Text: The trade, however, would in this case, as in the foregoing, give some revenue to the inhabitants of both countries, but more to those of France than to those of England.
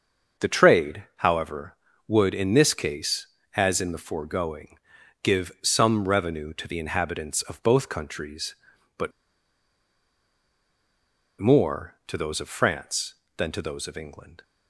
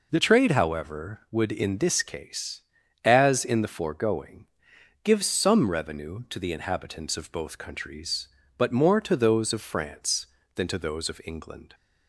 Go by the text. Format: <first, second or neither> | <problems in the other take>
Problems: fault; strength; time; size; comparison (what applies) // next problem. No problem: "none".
second | starts louder than the rest; until 1.5 s; 6 dB // pauses between "but" and "more"; strong; at 9.1 s; 2.2 s long